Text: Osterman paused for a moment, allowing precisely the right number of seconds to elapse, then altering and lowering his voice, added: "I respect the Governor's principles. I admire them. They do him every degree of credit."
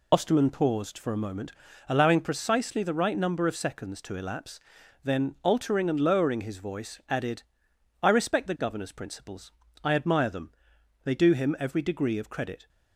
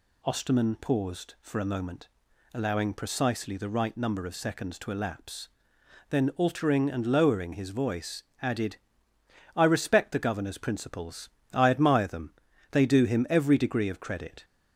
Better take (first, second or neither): second